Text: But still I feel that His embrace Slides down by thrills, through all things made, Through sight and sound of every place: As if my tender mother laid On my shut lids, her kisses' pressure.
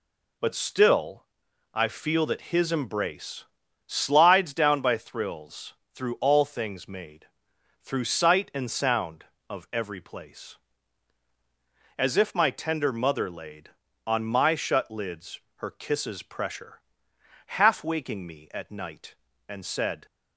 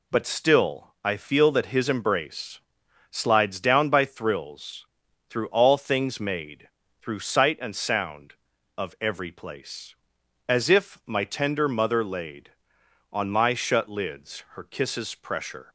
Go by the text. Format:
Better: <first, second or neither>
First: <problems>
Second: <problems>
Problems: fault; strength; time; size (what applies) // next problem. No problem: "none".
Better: second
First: pauses between "still" and "I"; noticeable; at 1.2 s; 0.50 s long // pauses between "embrace" and "Slides"; noticeable; at 3.4 s; 0.46 s long // goes on to say "Half waking me at night and said"; strong; from 17.4 s on; 2.5 s long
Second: pauses between "embrace" and "Slides"; noticeable; at 2.5 s; 0.52 s long